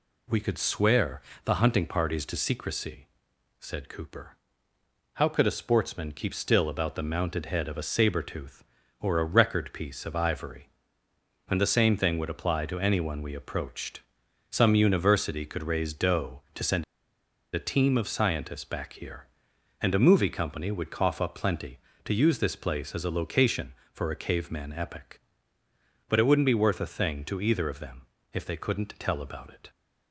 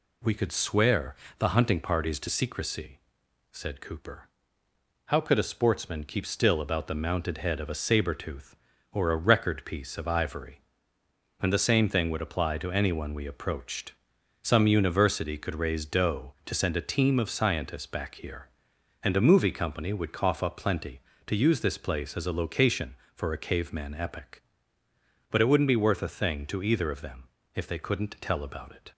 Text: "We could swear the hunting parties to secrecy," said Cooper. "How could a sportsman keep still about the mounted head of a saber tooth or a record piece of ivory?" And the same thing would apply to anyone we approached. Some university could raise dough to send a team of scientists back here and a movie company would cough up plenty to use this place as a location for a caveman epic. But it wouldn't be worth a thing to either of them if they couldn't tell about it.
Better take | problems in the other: second | pauses between "swear" and "the"; slight; at 1.2 s; 0.22 s long; slight in the second // pauses between "send" and "a"; noticeable; at 16.8 s; 0.69 s long // pauses between "them" and "if"; slight; at 28.0 s; 0.26 s long; slight in the second

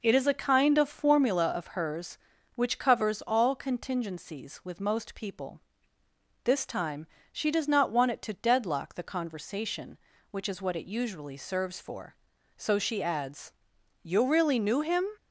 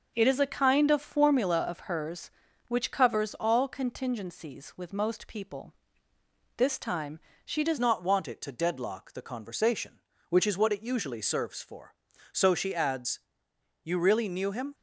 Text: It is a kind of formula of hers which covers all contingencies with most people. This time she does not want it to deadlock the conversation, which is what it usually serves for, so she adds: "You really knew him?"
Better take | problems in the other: first | pauses between "time" and "she"; slight; at 7.1 s; 0.26 s long; slight in the first // changes voice at "not"; from 7.7 s on; 7.0 s long

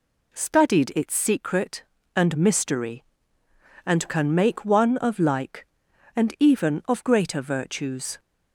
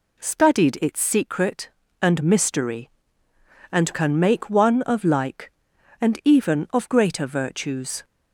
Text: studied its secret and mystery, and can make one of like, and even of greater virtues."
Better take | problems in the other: neither | none

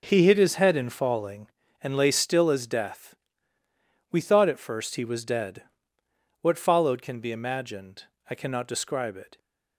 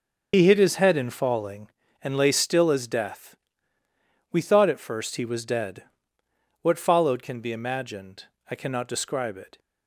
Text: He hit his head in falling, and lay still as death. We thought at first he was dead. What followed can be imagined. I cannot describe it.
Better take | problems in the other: first | loses the start of "He"; at 0.3 s; 100 ms // starts louder than the rest; until 1.3 s; 6.5 dB

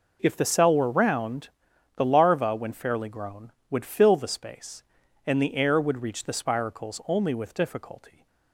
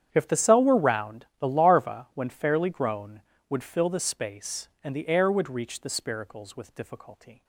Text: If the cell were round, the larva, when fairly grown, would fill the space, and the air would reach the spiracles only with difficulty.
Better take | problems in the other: first | starts louder than the rest; strong; until 1.1 s; 9 dB // skips "only"; at 6.5 s

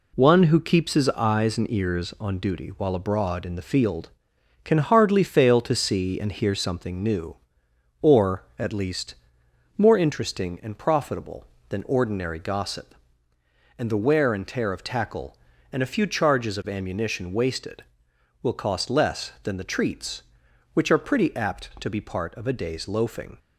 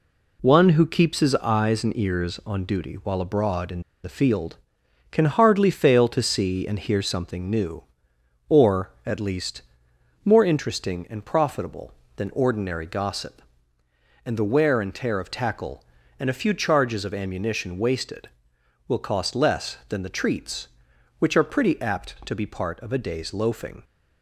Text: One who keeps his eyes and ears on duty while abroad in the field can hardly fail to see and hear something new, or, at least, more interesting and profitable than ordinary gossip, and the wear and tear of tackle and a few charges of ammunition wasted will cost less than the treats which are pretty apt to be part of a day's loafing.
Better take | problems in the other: first | pauses between "in" and "the"; slight; at 3.8 s; 0.21 s long

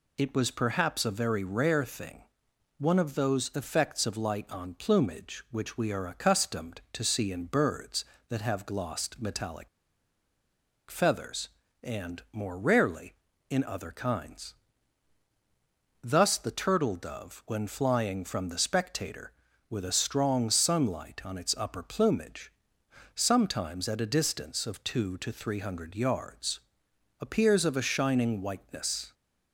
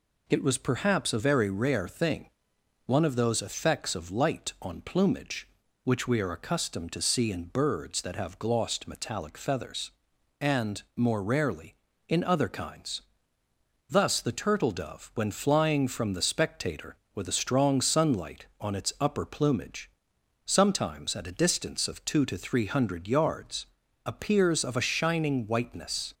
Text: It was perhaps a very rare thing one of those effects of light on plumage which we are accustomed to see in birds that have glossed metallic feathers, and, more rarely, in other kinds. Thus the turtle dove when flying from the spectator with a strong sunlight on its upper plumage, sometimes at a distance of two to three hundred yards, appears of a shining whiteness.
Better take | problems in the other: second | pauses between "thing" and "one"; noticeable; at 2.2 s; 0.54 s long; noticeable in the second // pauses between "metallic" and "feathers"; at 9.6 s; 1.2 s long

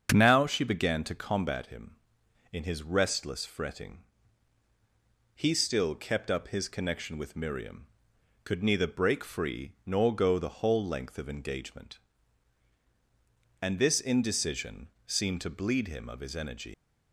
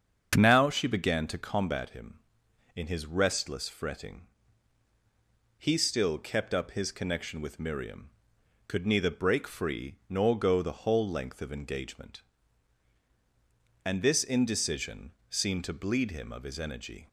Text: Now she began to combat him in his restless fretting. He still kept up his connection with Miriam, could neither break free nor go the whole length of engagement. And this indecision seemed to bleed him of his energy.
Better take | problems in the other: second | starts louder than the rest; until 1.1 s; 7 dB; also in the second // pauses between "indecision" and "seemed"; slight; at 14.8 s; 0.18 s long; slight in the second // leaves "energy" unfinished; at 16.7 s; 105 ms

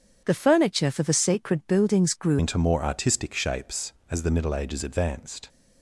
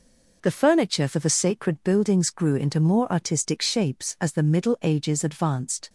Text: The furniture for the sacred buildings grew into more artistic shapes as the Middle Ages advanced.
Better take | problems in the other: second | starts louder than the rest; strong; until 1.2 s; 7.5 dB // changes voice at "into"; from 2.3 s on; 3.1 s long

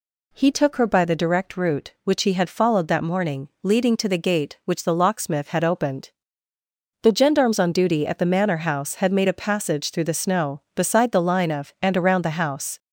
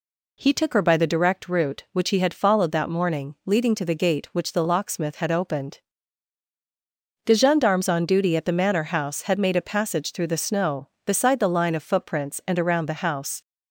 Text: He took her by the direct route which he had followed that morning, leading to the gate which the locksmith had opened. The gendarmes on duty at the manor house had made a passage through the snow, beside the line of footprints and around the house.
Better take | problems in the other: second | skips "footprints"; at 11.7 s

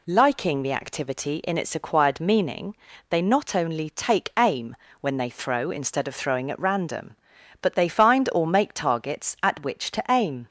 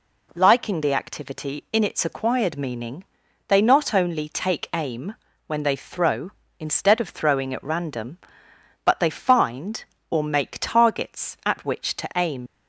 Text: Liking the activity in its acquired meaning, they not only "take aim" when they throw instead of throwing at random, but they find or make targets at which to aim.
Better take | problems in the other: first | pauses between "aim" and "when"; slight; at 5.1 s; 0.32 s long; slight in the first // leaves "aim" unfinished; at 12.4 s; 75 ms

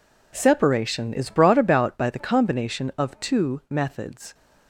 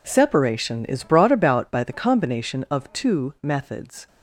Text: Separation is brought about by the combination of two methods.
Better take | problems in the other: neither | none

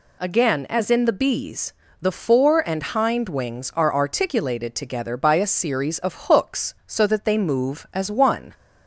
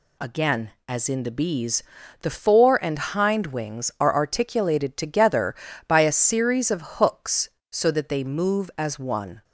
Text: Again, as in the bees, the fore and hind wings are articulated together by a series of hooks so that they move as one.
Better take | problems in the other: neither | none

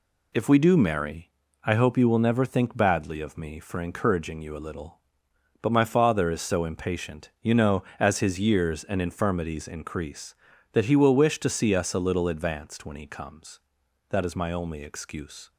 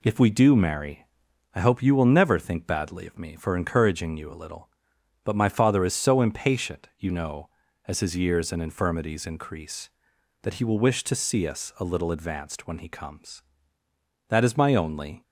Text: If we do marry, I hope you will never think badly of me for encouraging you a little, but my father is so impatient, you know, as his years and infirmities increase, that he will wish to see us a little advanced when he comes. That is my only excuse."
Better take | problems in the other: first | stops before "excuse"; at 15.2 s

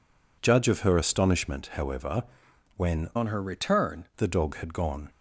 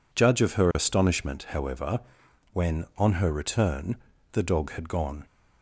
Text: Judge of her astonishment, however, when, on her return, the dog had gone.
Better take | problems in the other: second | changes voice from "on" to "return"; from 3.1 to 4.0 s; 0.9 s long

